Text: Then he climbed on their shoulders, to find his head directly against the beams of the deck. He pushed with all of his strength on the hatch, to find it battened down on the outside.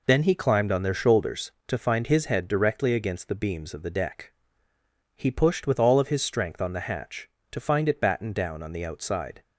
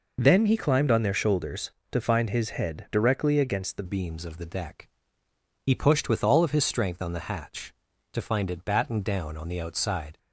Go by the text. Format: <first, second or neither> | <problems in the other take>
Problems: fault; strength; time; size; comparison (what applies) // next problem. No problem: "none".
first | changes voice at "beams"; from 3.8 s on; 6.3 s long